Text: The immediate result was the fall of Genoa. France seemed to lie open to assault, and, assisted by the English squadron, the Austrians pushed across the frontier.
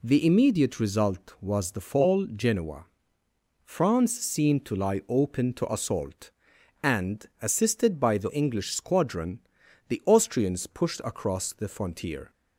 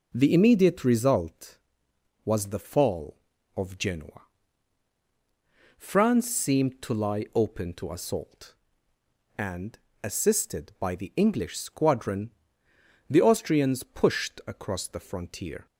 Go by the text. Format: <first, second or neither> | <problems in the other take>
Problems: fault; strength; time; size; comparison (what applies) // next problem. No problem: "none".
second | skips "of"; at 2.2 s